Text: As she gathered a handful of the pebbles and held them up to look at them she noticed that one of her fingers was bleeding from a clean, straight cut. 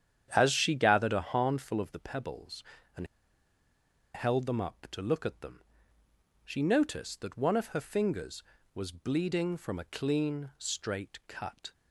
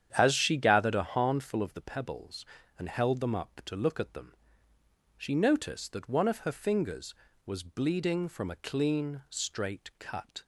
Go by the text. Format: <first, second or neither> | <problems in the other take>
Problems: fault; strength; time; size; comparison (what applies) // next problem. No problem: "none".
second | starts louder than the rest; strong; until 1.3 s; 9 dB; strong in the second // pauses between "and" and "held"; at 3.0 s; 1.0 s long // pauses between "them" and "she"; noticeable; at 5.6 s; 0.82 s long; noticeable in the second